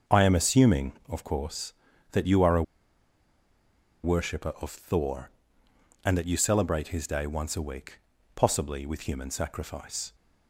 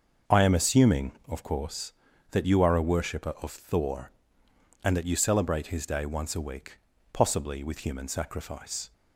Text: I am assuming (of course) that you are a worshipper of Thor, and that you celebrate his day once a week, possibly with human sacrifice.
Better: second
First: starts louder than the rest; until 1.2 s; 6.5 dB // pauses between "a" and "worshipper"; strong; at 2.6 s; 1.4 s long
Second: starts louder than the rest; until 1.4 s; 6.5 dB

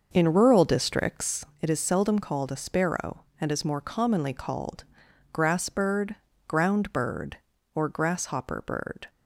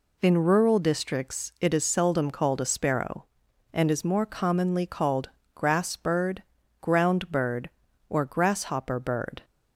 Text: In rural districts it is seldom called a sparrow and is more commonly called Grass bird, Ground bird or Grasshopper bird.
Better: second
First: starts louder than the rest; noticeable; until 1.6 s; 6 dB // pauses between "districts" and "it"; slight; at 1.4 s; 0.16 s long // pauses between "called" and "Grass"; noticeable; at 4.8 s; 0.48 s long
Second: pauses between "called" and "Grass"; slight; at 5.2 s; 0.24 s long

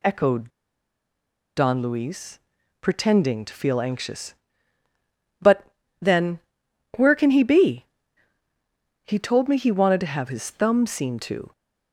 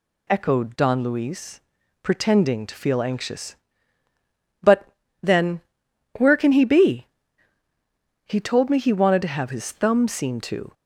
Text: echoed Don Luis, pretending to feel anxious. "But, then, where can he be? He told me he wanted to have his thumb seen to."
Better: second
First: pauses between "echoed" and "Don"; at 0.4 s; 1.0 s long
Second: none

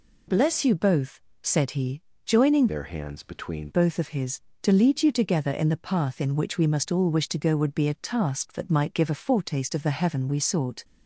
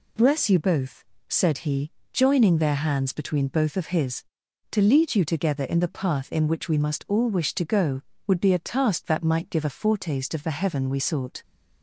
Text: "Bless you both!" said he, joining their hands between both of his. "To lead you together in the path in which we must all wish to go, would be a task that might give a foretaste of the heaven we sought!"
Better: second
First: changes voice from "their" to "between"; from 2.6 to 3.6 s; 1.0 s long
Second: none

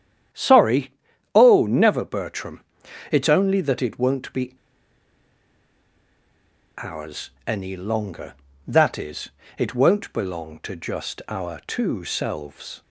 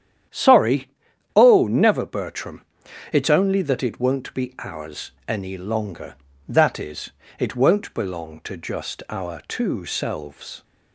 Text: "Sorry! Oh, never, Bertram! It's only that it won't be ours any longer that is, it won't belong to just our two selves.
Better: second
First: starts louder than the rest; strong; until 1.7 s; 9.5 dB // pauses between "be" and "ours"; strong; at 4.5 s; 2.2 s long // pauses between "ours" and "any"; slight; at 7.2 s; 0.18 s long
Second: starts louder than the rest; strong; until 1.7 s; 9.5 dB // pauses between "ours" and "any"; slight; at 5.1 s; 0.18 s long

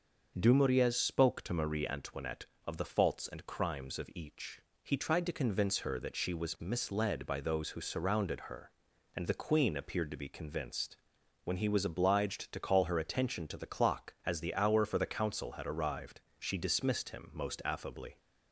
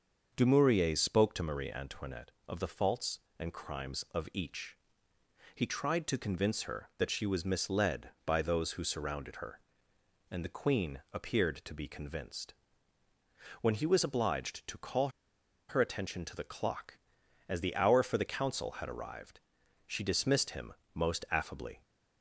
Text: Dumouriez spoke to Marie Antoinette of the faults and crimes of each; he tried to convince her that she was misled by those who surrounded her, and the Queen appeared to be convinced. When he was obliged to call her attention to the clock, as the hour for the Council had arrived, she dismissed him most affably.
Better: first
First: starts louder than the rest; noticeable; until 1.3 s; 6 dB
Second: starts louder than the rest; until 1.3 s; 6.5 dB // pauses between "call" and "her"; noticeable; at 15.0 s; 0.60 s long // pauses between "him" and "most"; slight; at 20.7 s; 0.22 s long

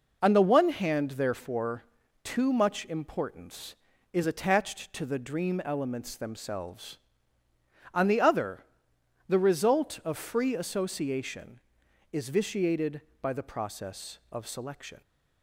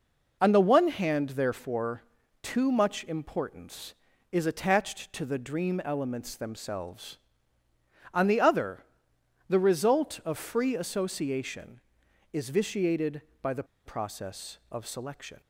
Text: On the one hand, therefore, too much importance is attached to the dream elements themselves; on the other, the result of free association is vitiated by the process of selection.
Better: first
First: none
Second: pauses between "the" and "process"; slight; at 13.6 s; 0.22 s long

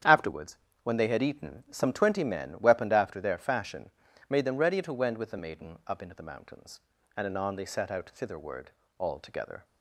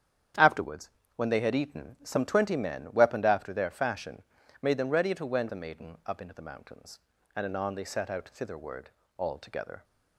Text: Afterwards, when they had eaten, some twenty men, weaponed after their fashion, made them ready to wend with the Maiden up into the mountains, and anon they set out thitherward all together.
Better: first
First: starts louder than the rest; strong; until 1.3 s; 9 dB // pauses between "thitherward" and "all"; slight; at 8.7 s; 0.26 s long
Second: starts louder than the rest; strong; until 1.6 s; 9 dB // skips "with"; at 5.4 s // pauses between "thitherward" and "all"; slight; at 8.9 s; 0.26 s long

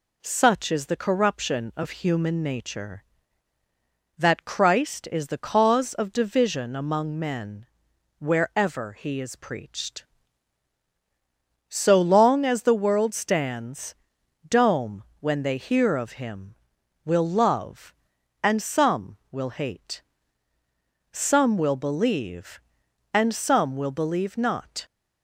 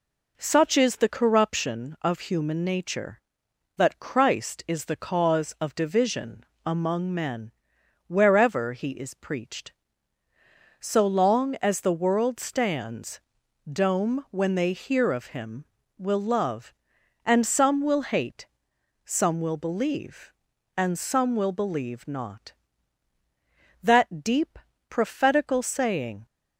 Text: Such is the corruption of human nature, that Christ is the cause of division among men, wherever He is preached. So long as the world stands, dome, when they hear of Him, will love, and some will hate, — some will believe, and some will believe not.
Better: first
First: none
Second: pauses between "division" and "among"; slight; at 6.4 s; 0.20 s long // goes on to say "That deep prophetical saying"; strong; from 23.8 s on; 2.4 s long

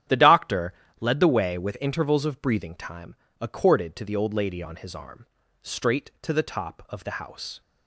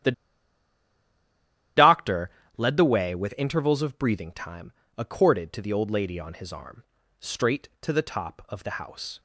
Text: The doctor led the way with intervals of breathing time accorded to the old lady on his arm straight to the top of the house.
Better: first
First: starts louder than the rest; strong; until 1.3 s; 10 dB // pauses between "doctor" and "led"; slight; at 0.7 s; 0.26 s long // pauses between "time" and "accorded"; slight; at 3.1 s; 0.26 s long // pauses between "arm" and "straight"; slight; at 5.2 s; 0.36 s long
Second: starts louder than the rest; strong; until 2.9 s; 11 dB // pauses between "The" and "doctor"; strong; at 0.1 s; 1.6 s long // pauses between "doctor" and "led"; slight; at 2.2 s; 0.26 s long // pauses between "time" and "accorded"; slight; at 4.7 s; 0.26 s long // pauses between "arm" and "straight"; slight; at 6.8 s; 0.36 s long

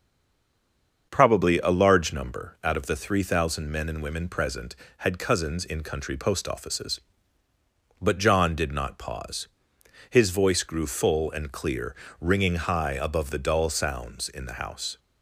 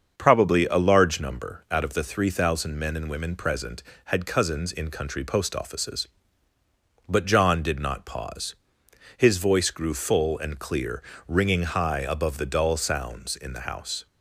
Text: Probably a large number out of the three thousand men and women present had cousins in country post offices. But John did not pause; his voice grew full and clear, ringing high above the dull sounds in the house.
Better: second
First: stays silent before the first word; until 1.1 s; 1.1 s long // starts louder than the rest; until 2.1 s; 7 dB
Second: starts louder than the rest; until 1.1 s; 7 dB

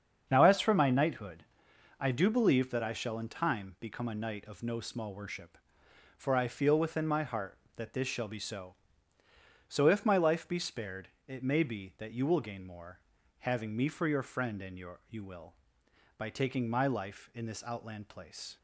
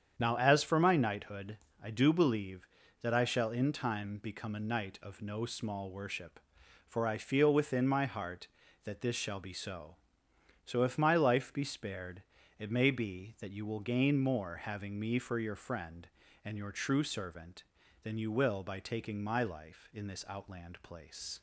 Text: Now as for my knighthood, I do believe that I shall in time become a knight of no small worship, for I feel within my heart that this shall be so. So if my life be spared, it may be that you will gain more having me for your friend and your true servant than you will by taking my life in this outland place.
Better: second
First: starts louder than the rest; strong; until 1.3 s; 7 dB // pauses between "more" and "having"; at 12.9 s; 0.42 s long // skips "true servant than"; at 15.0 s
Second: starts louder than the rest; strong; until 1.1 s; 8 dB

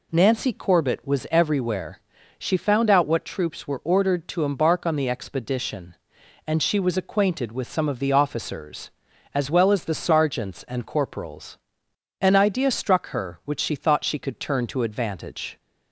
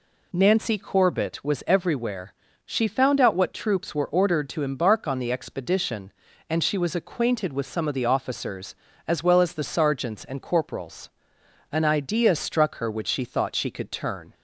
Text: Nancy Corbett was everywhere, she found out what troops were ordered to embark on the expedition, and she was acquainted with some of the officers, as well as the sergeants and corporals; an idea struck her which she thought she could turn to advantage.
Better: first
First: none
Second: stops before "to advantage"; at 14.3 s

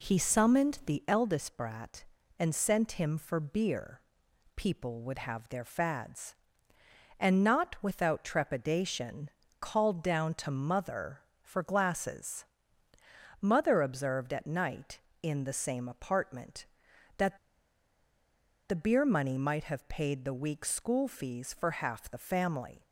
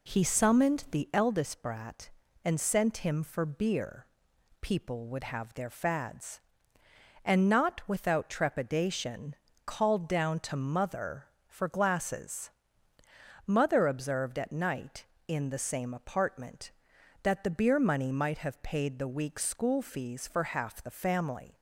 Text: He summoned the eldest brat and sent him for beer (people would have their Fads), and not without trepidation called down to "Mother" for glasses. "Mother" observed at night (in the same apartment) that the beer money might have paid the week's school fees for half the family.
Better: second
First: pauses between "trepidation" and "called"; slight; at 9.2 s; 0.30 s long // pauses between "that" and "the"; strong; at 17.3 s; 1.3 s long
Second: pauses between "trepidation" and "called"; slight; at 9.3 s; 0.30 s long

